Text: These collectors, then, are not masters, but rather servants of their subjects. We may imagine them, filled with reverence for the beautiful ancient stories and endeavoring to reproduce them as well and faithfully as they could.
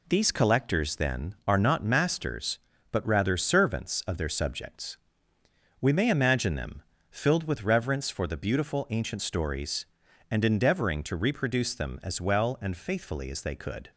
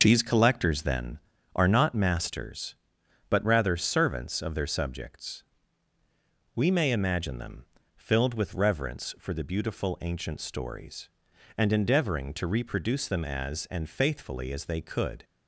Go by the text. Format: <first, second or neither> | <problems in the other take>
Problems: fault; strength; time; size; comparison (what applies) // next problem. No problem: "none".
first | skips "well"; at 13.6 s